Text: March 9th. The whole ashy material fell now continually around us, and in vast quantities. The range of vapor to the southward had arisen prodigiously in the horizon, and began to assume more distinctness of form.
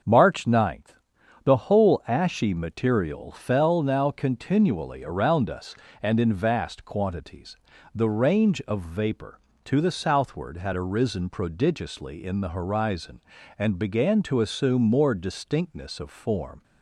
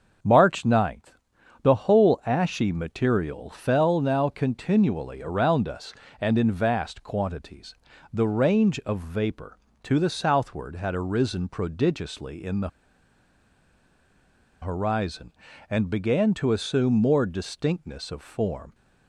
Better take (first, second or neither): first